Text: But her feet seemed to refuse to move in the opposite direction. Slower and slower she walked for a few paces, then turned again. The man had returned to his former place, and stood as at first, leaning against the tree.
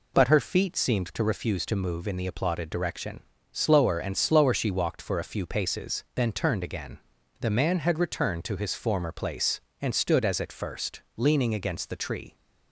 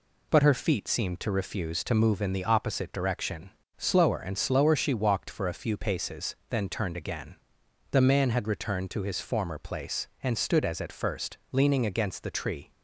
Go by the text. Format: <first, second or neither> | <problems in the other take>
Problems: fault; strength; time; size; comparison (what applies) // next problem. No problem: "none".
second | says "applauded" for "opposite"; at 2.2 s